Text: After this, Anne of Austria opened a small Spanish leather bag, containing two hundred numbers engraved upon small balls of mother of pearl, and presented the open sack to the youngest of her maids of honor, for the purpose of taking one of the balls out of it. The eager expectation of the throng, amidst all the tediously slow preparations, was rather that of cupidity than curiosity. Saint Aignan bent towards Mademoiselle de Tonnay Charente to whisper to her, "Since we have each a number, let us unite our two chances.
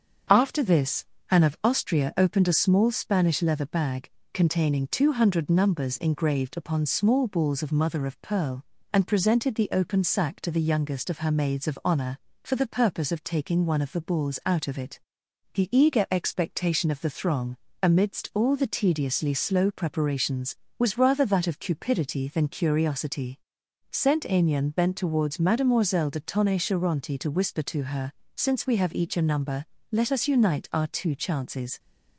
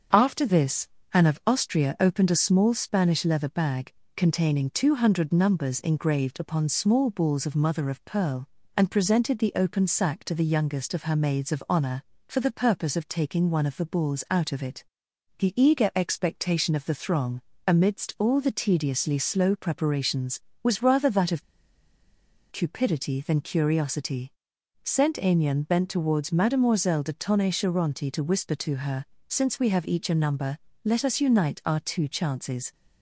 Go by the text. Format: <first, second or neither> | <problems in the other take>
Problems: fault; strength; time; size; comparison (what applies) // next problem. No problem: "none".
first | starts louder than the rest; until 1.3 s; 6.5 dB; also in the first // pauses between "of" and "cupidity"; at 21.4 s; 1.1 s long